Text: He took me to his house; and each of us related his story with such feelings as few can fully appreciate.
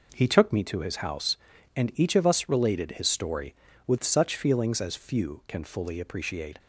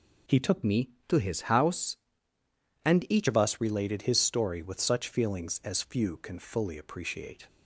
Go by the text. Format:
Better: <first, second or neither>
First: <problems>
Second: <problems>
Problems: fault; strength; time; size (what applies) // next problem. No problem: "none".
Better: first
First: none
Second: changes voice from "me" to "each"; from 0.6 to 3.2 s; 2.6 s long